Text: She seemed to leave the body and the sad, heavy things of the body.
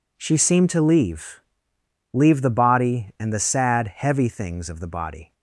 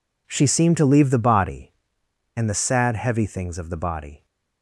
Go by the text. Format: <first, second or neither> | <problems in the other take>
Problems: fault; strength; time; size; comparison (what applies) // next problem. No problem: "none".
second | says "leave" twice; at 2.1 s